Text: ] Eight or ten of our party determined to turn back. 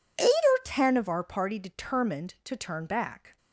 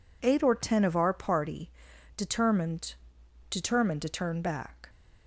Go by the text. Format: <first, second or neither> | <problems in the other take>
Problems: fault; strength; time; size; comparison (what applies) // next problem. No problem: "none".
first | pauses between "party" and "determined"; noticeable; at 1.6 s; 0.46 s long // says "determined" twice; at 3.5 s